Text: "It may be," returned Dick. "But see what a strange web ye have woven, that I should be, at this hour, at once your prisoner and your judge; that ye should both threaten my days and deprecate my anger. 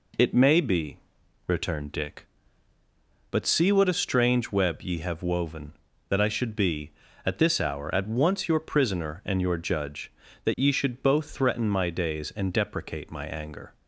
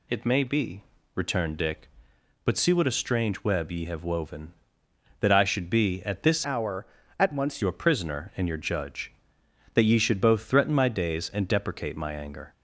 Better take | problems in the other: first | changes voice from "hour" to "once"; from 6.4 to 7.6 s; 1.2 s long

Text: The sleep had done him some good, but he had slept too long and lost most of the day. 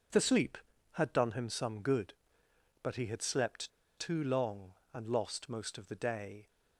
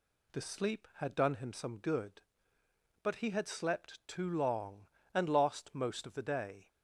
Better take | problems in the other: second | pauses between "slept" and "too"; slight; at 3.7 s; 0.27 s long

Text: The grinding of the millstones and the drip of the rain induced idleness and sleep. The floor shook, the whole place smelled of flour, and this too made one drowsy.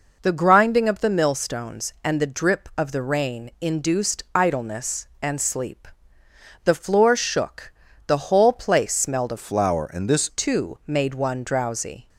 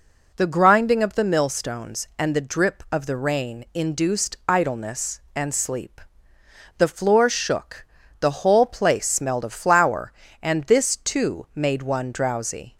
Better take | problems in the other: second | changes voice from "flour" to "this"; from 9.3 to 10.2 s; 0.9 s long

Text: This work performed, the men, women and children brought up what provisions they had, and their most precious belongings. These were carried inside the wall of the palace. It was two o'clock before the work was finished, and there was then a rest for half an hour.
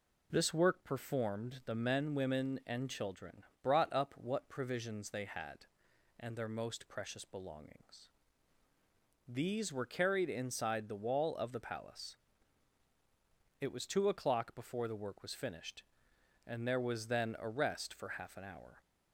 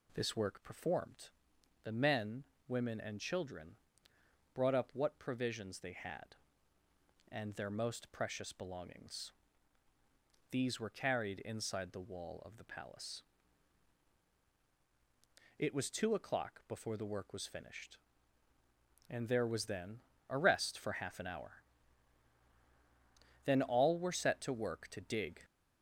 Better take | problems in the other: first | pauses between "children" and "brought"; noticeable; at 3.7 s; 0.78 s long; slight in the first // pauses between "then" and "a"; slight; at 19.9 s; 0.30 s long // goes on to say "Then all were set to work to dig"; strong; from 23.4 s on; 1.9 s long

